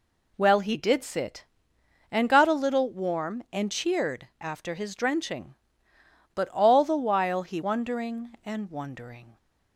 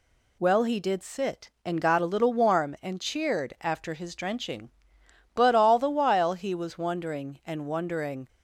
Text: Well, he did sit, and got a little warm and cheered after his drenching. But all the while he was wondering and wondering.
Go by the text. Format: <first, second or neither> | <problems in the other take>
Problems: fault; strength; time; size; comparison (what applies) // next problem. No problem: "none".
second | skips "was"; at 7.6 s